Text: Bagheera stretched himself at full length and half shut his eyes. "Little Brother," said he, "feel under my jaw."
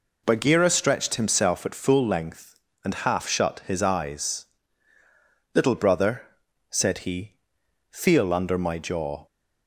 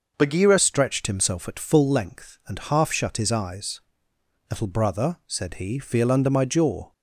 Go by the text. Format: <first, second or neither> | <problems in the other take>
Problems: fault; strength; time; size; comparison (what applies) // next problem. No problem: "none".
first | changes voice at "stretched"; from 0.5 s on; 6.4 s long